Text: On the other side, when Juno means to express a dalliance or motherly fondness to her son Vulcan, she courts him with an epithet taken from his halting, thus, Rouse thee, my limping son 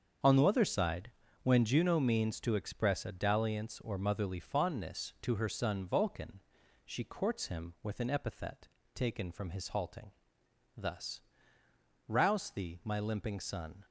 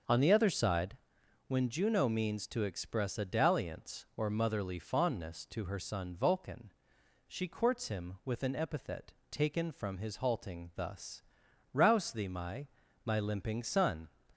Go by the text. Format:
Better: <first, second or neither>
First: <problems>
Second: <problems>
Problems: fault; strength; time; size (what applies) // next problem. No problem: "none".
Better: first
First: starts louder than the rest; strong; until 1.5 s; 7 dB // pauses between "epithet" and "taken"; slight; at 8.6 s; 0.28 s long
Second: starts louder than the rest; until 1.5 s; 6 dB // pauses between "epithet" and "taken"; slight; at 9.1 s; 0.18 s long // says "my" twice; at 13.0 s